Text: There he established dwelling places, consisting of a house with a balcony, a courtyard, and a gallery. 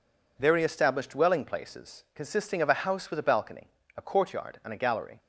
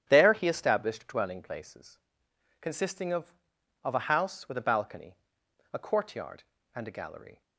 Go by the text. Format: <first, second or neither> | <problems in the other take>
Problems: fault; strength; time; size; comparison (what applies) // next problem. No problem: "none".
first | starts louder than the rest; strong; until 1.0 s; 10 dB // says "of" twice; at 3.8 s